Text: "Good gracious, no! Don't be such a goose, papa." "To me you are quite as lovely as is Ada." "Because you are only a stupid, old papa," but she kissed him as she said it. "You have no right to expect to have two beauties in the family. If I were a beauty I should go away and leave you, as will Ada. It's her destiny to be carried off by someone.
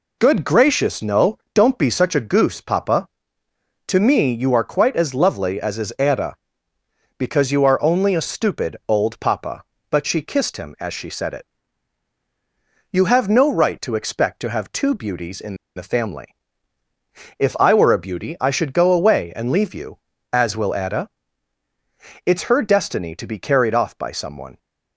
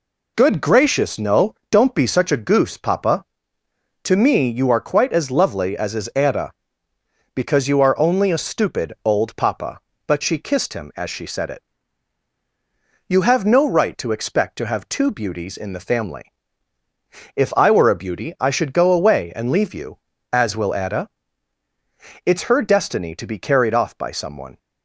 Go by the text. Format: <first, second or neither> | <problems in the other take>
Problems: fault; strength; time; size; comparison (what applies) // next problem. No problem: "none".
second | pauses between "in" and "the"; slight; at 15.5 s; 0.21 s long